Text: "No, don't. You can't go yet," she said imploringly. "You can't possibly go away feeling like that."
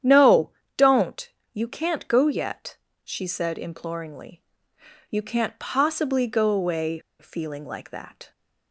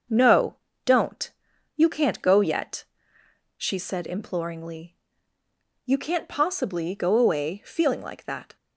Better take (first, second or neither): second